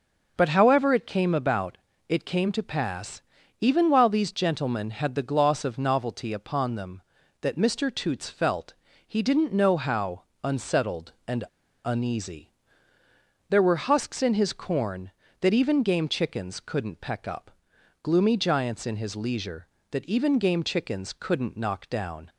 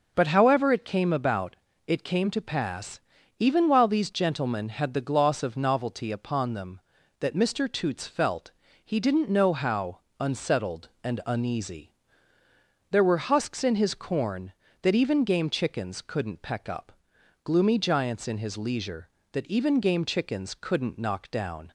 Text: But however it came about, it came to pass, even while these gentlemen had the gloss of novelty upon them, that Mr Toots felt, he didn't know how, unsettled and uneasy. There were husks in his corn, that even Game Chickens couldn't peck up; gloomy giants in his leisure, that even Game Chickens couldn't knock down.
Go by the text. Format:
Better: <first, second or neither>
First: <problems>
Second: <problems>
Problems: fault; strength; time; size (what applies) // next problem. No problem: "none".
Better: second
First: starts louder than the rest; until 1.3 s; 6 dB // pauses between "and" and "uneasy"; at 11.4 s; 0.40 s long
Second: starts louder than the rest; noticeable; until 1.1 s; 6 dB